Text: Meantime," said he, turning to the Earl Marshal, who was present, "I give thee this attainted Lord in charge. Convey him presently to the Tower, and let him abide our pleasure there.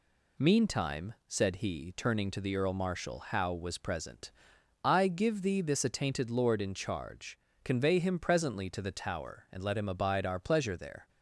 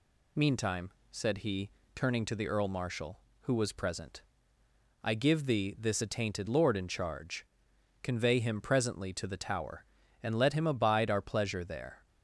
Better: second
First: says "how" for "who"; at 3.1 s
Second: none

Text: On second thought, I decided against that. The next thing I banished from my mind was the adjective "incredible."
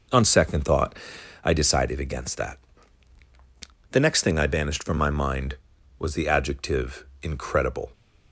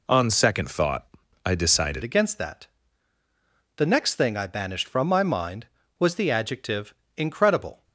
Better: first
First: pauses between "adjective" and "incredible"; slight; at 7.0 s; 0.18 s long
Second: changes voice at "against"; from 2.0 s on; 5.8 s long // pauses between "adjective" and "incredible"; slight; at 6.9 s; 0.24 s long

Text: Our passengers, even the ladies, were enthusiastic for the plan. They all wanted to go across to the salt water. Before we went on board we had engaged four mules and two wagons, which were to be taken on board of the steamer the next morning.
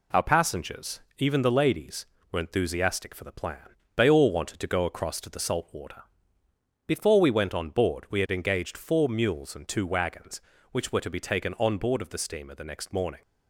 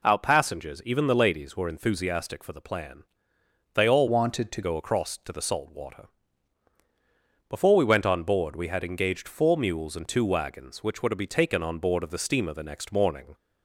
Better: first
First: none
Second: changes voice from "wanted" to "to"; from 4.0 to 4.6 s; 0.6 s long

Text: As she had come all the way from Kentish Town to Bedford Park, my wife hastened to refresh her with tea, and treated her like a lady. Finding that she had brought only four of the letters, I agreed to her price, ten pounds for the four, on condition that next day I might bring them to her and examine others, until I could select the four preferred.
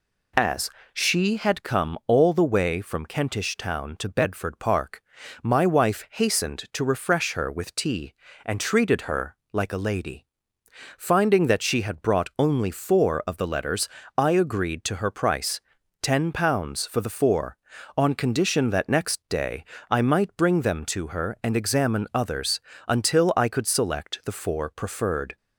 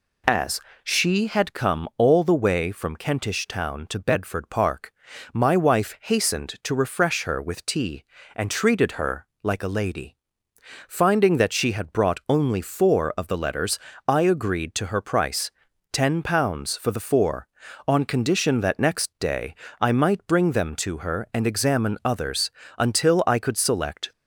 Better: first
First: pauses between "As" and "she"; slight; at 0.6 s; 0.24 s long // pauses between "her" and "like"; slight; at 9.3 s; 0.16 s long // pauses between "day" and "I"; slight; at 19.6 s; 0.26 s long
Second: pauses between "As" and "she"; slight; at 0.5 s; 0.24 s long // pauses between "her" and "like"; slight; at 9.2 s; 0.16 s long // pauses between "day" and "I"; slight; at 19.5 s; 0.26 s long // stops before "the four preferred"; at 24.1 s

